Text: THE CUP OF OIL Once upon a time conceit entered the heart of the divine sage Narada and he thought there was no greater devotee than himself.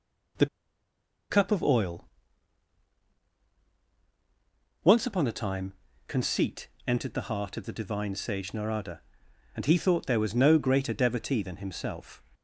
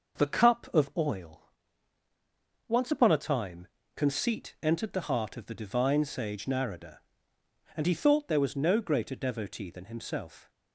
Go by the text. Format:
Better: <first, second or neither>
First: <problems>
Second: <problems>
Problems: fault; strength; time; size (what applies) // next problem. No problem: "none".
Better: second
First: pauses between "THE" and "CUP"; noticeable; at 0.4 s; 0.83 s long // pauses between "OIL" and "Once"; strong; at 2.0 s; 2.8 s long // pauses between "time" and "conceit"; slight; at 5.7 s; 0.36 s long // pauses between "conceit" and "entered"; slight; at 6.6 s; 0.18 s long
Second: pauses between "OIL" and "Once"; at 1.5 s; 1.1 s long // pauses between "time" and "conceit"; slight; at 3.6 s; 0.30 s long